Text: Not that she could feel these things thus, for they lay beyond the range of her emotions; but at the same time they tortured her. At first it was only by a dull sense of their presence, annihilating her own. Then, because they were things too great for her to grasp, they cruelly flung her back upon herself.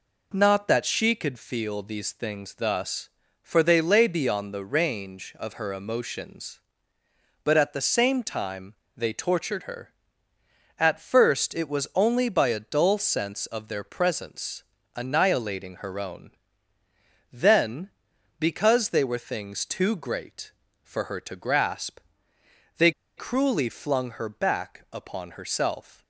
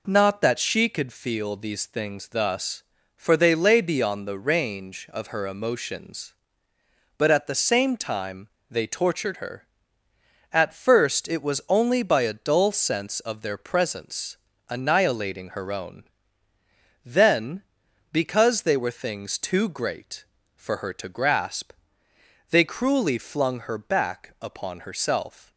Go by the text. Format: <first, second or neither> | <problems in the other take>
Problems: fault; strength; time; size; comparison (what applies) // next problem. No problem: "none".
second | pauses between "time" and "they"; slight; at 8.7 s; 0.24 s long; slight in the second // pauses between "they" and "cruelly"; slight; at 22.9 s; 0.26 s long